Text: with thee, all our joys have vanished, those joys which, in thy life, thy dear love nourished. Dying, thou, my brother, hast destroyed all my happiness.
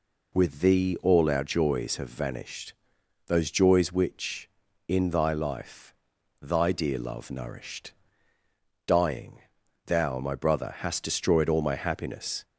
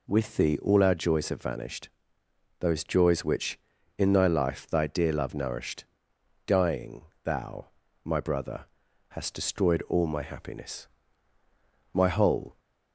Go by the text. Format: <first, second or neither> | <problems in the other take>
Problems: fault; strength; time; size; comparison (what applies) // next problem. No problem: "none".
first | goes on to say "My whole"; noticeable; from 11.9 s on; 0.66 s long